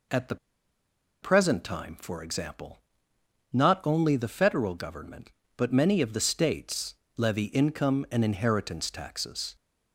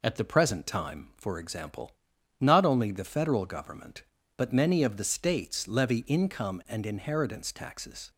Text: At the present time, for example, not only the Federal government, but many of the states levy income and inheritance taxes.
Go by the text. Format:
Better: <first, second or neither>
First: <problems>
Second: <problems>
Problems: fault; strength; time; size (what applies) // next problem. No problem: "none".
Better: second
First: pauses between "the" and "present"; noticeable; at 0.3 s; 0.86 s long // pauses between "states" and "levy"; slight; at 6.9 s; 0.20 s long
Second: none